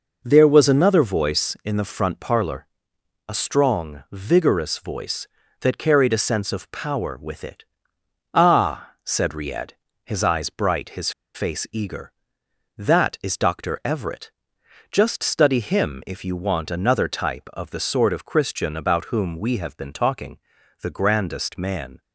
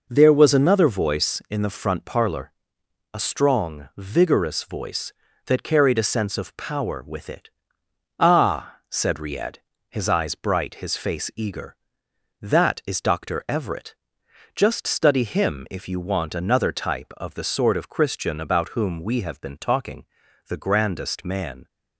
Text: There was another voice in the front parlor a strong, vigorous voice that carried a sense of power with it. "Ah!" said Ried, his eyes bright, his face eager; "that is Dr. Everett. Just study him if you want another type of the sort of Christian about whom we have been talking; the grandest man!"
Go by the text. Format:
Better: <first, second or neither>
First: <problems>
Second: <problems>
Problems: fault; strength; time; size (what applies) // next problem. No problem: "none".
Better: second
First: pauses between "parlor" and "a"; noticeable; at 2.6 s; 0.60 s long // pauses between "his" and "face"; slight; at 11.1 s; 0.24 s long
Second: pauses between "parlor" and "a"; noticeable; at 2.5 s; 0.60 s long